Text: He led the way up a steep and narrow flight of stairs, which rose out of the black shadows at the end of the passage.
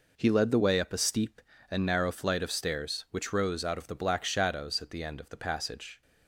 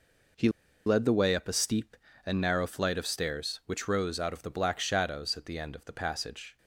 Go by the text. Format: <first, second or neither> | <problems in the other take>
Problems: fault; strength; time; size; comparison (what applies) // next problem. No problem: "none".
first | pauses between "He" and "led"; at 0.4 s; 0.37 s long